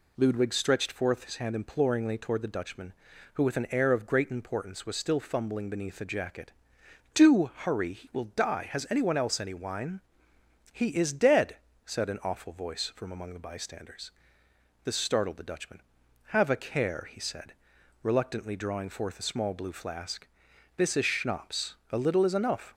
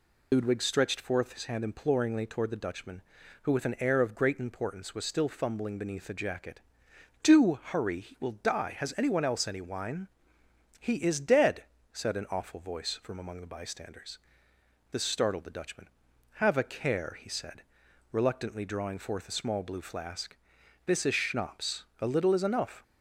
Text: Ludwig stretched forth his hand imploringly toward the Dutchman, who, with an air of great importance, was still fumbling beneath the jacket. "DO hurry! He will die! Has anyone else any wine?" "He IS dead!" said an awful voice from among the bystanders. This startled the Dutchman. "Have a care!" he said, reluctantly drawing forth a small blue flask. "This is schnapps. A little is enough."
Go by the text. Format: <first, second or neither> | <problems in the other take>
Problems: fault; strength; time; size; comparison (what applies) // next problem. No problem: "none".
first | loses the start of "Ludwig"; at 0.3 s; 65 ms